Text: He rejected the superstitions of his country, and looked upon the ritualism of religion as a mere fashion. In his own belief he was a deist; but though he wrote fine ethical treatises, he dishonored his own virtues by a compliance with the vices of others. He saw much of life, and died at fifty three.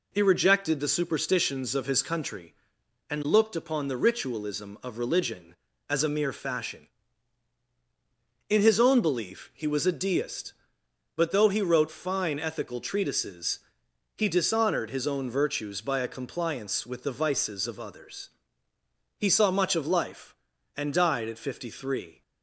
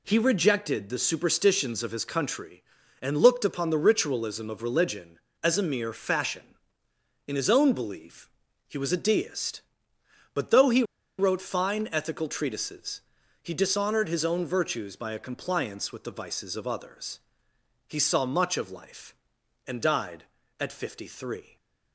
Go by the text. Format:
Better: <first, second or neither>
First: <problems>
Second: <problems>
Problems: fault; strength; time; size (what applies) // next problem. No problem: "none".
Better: first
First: none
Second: pauses between "belief" and "he"; at 8.2 s; 0.38 s long // pauses between "he" and "wrote"; slight; at 10.8 s; 0.35 s long // stays silent after the last word; slight; from 21.4 s on; 0.5 s long